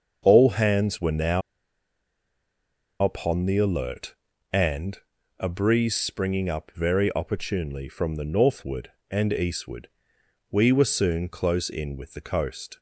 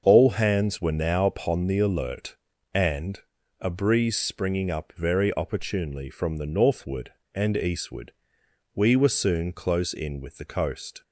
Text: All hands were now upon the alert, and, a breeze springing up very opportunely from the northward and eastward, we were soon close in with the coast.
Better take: second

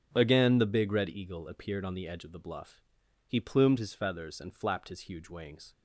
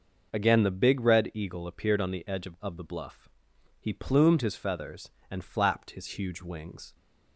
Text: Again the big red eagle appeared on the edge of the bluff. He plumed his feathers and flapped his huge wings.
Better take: first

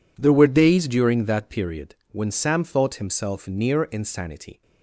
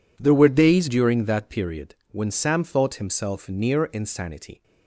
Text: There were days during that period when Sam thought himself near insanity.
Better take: neither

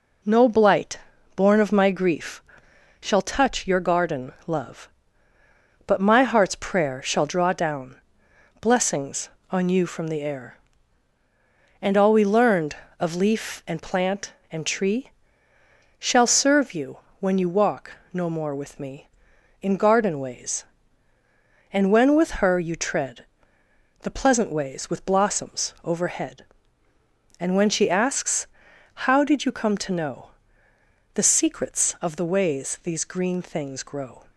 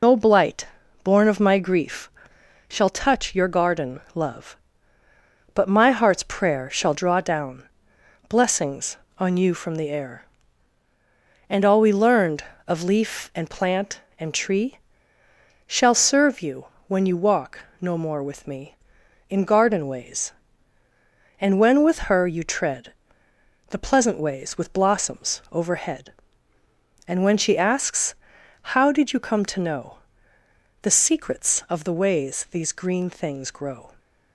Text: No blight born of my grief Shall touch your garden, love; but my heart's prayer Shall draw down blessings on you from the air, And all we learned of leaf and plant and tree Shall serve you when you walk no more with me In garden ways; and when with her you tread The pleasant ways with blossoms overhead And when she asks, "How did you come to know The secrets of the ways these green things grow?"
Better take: first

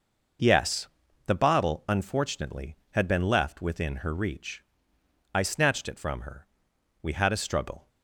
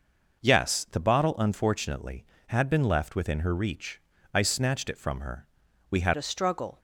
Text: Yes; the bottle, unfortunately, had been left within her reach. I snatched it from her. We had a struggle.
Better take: first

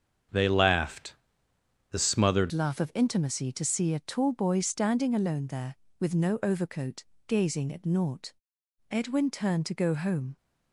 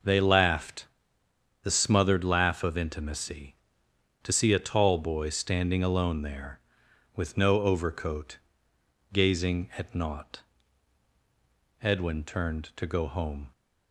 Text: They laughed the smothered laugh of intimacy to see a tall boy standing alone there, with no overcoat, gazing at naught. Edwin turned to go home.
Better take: second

